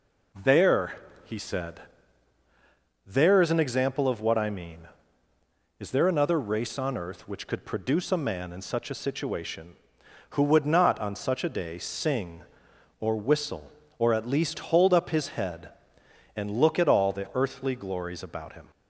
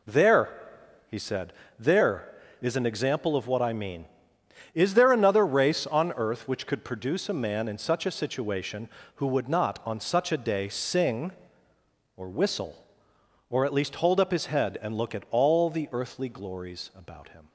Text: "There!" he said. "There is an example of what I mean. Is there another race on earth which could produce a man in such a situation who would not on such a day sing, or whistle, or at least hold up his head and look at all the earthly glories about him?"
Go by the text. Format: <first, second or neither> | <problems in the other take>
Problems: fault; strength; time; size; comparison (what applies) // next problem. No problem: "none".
neither | none